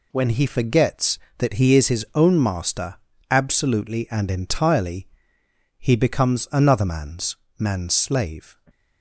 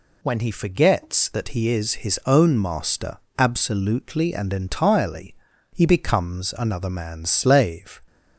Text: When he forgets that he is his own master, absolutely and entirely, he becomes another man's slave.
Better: second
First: says "man's" twice; at 7.5 s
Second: none

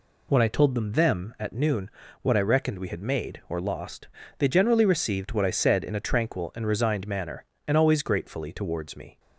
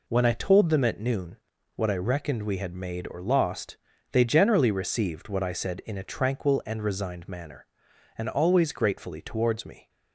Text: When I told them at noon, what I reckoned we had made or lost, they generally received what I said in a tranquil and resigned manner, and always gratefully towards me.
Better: second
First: says "them" twice; at 0.9 s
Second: none

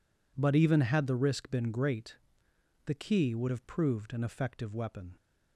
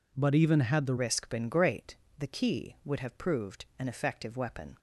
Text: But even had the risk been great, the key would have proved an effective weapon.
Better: first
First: none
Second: changes voice at "risk"; from 0.9 s on; 3.8 s long

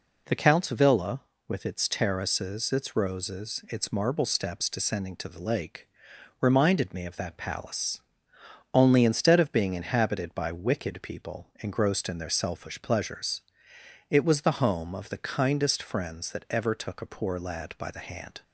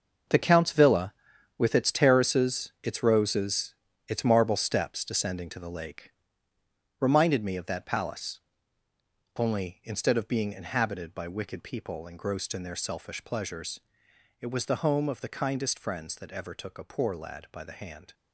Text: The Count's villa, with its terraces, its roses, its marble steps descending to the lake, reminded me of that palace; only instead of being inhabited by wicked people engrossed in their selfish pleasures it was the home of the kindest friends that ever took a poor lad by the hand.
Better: first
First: pauses between "pleasures" and "it"; noticeable; at 13.4 s; 0.70 s long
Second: gets quieter; strong; throughout; 10.5 dB // pauses between "pleasures" and "it"; noticeable; at 13.7 s; 0.62 s long

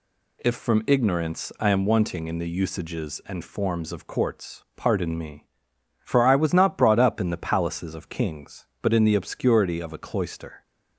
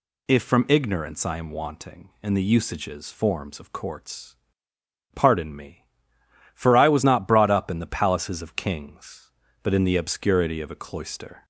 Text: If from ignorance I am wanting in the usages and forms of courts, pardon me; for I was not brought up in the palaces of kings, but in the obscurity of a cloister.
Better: first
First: none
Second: skips "and"; at 3.1 s

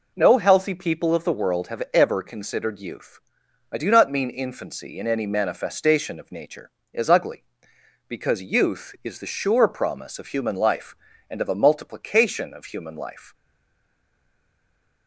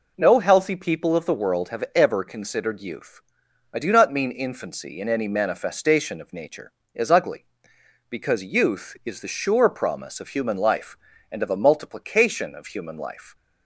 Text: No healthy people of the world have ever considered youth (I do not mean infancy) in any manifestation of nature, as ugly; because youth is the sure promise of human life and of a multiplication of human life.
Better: second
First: stays silent after the last word; noticeable; from 13.3 s on; 1.7 s long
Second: none

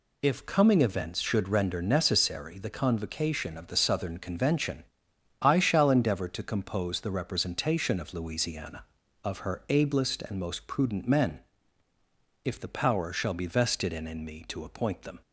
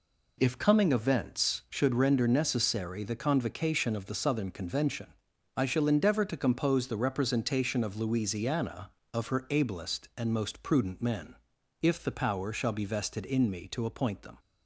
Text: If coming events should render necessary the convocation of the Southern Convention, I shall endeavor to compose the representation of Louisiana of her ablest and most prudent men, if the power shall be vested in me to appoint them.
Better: second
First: says "in" twice; at 14.0 s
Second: none

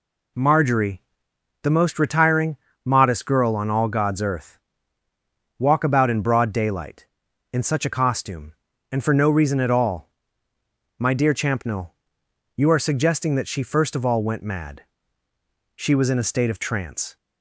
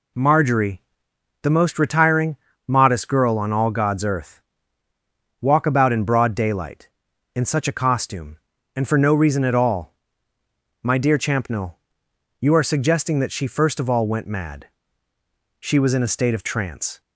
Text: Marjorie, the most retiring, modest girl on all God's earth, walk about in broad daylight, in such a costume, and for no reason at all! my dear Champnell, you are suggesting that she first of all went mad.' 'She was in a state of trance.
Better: neither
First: none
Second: none

